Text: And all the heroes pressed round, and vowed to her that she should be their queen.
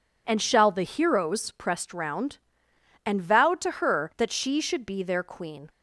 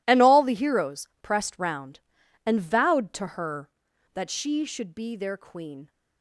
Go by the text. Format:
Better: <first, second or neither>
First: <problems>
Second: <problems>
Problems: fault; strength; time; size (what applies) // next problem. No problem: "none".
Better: second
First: says "shall" for "all"; at 0.4 s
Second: none